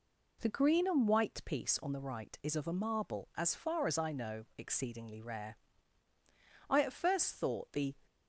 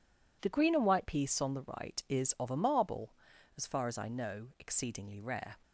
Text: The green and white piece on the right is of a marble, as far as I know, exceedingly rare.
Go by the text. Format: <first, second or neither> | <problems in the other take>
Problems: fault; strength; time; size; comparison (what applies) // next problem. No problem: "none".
second | goes on to say "I at first thought the"; noticeable; from 6.6 s on; 1.2 s long